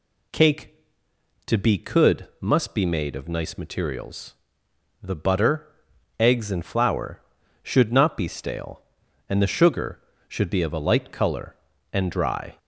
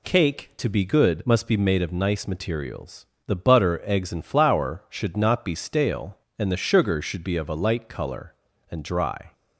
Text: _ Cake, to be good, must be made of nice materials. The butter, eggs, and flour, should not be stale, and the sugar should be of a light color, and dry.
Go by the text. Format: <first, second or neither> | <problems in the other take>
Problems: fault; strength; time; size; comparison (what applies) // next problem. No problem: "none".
second | says "could" for "good"; at 1.7 s